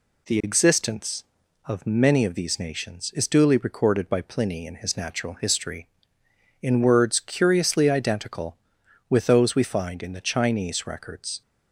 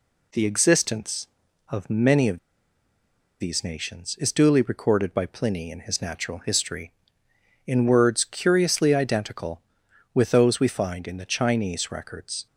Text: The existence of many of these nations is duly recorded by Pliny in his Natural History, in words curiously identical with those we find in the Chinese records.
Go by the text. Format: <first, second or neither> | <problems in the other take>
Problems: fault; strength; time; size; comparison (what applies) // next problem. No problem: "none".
first | pauses between "of" and "these"; at 2.3 s; 1.0 s long